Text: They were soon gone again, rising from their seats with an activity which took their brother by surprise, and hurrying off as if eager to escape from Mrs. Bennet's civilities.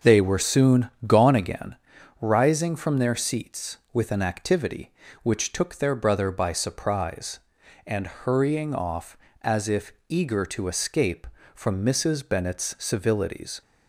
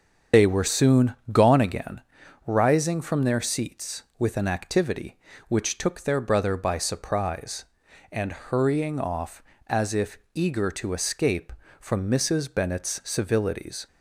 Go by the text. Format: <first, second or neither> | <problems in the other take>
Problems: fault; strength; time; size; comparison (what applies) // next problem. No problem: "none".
first | loses the start of "They"; at 0.3 s; 50 ms // starts louder than the rest; strong; until 1.5 s; 7 dB; also in the first // pauses between "soon" and "gone"; slight; at 1.1 s; 0.16 s long; slight in the first // pauses between "if" and "eager"; slight; at 10.1 s; 0.16 s long; slight in the first